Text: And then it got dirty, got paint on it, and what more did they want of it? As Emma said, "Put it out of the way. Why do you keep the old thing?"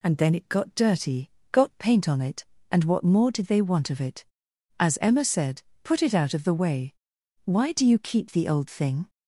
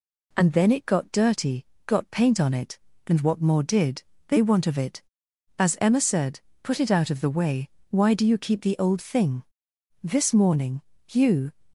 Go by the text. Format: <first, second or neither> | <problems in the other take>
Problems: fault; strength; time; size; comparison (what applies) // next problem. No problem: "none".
first | pauses between "did" and "they"; slight; at 4.0 s; 0.26 s long // goes on to say "This morning you"; from 10.0 s on; 1.5 s long